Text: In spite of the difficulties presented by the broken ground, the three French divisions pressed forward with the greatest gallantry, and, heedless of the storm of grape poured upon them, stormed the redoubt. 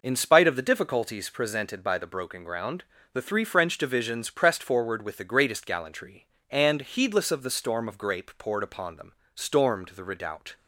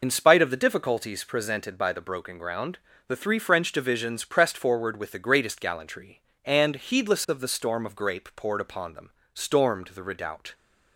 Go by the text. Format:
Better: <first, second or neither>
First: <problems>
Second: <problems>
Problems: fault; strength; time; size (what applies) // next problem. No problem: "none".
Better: first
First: none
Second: loses the start of "In"; at 0.0 s; 55 ms